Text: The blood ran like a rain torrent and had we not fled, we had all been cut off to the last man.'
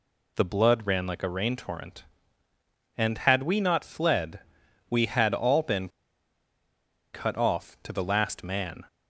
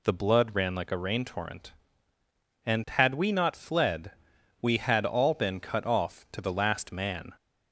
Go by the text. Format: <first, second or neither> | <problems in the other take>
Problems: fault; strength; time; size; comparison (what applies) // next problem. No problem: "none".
second | pauses between "been" and "cut"; strong; at 5.8 s; 1.2 s long